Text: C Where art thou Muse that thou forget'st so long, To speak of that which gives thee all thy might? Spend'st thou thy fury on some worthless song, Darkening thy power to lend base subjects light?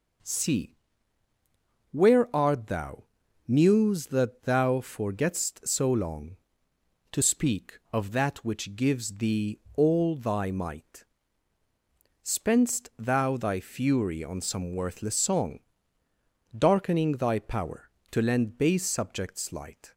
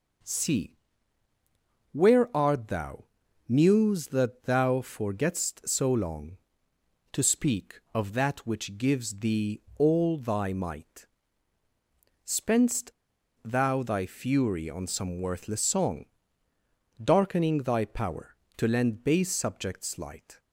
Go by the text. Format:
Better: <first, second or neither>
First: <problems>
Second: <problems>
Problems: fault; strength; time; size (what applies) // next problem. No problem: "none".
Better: first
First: pauses between "C" and "Where"; at 0.7 s; 1.1 s long // pauses between "thou" and "Muse"; at 3.0 s; 0.44 s long // pauses between "thee" and "all"; slight; at 9.5 s; 0.16 s long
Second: pauses between "C" and "Where"; at 0.7 s; 1.1 s long // pauses between "thou" and "Muse"; at 3.0 s; 0.44 s long // pauses between "thee" and "all"; slight; at 9.6 s; 0.16 s long // pauses between "Spend'st" and "thou"; noticeable; at 12.9 s; 0.54 s long